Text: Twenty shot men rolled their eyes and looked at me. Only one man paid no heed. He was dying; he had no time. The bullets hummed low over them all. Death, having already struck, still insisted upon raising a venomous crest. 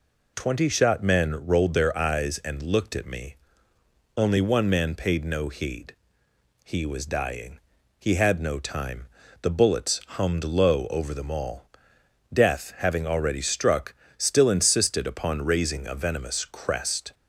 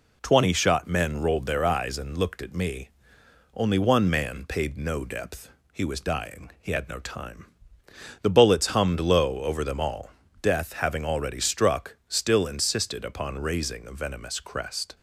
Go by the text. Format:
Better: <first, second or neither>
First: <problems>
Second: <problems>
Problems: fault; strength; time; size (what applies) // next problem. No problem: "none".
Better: first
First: none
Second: says "depth" for "heed"; at 5.0 s